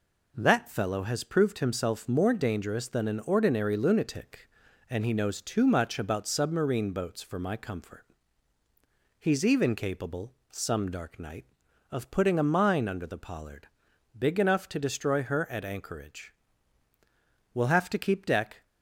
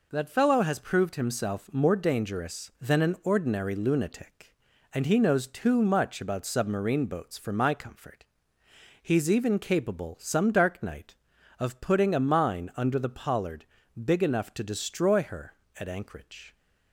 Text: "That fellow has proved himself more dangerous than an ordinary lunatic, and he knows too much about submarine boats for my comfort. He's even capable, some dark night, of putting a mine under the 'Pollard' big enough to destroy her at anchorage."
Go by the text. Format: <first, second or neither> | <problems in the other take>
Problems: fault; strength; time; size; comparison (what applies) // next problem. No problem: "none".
second | pauses between "Pollard" and "big"; noticeable; at 13.6 s; 0.50 s long; also in the second // goes on to say "We'll have to keep deck"; noticeable; from 17.5 s on; 1.1 s long